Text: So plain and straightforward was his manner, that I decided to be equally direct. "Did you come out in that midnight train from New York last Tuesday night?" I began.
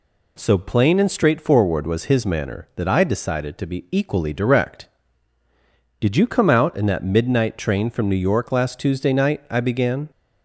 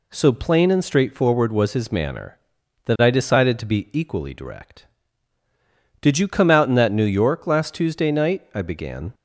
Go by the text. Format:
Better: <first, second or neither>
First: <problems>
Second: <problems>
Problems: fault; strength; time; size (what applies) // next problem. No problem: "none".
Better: first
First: none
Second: skips "midnight train from"; at 6.9 s